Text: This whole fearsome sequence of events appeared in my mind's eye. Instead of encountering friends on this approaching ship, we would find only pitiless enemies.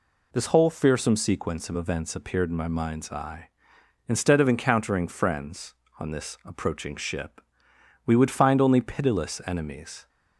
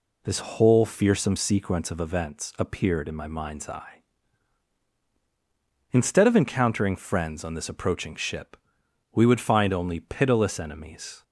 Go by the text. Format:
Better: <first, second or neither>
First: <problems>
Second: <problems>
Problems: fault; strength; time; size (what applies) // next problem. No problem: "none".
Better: neither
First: none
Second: none